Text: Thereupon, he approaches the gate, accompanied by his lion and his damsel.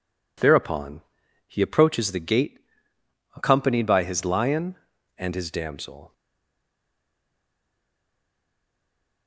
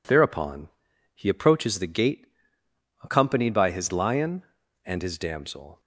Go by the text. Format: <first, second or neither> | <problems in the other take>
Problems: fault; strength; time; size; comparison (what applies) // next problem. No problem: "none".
second | stays silent after the last word; strong; from 6.1 s on; 3.1 s long